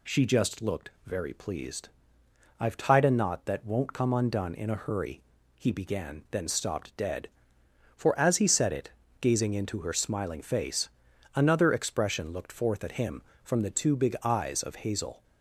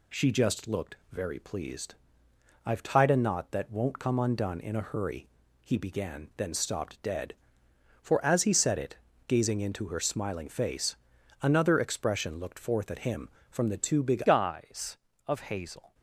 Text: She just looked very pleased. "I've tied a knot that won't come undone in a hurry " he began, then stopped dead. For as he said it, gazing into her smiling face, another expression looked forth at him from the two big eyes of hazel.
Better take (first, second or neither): first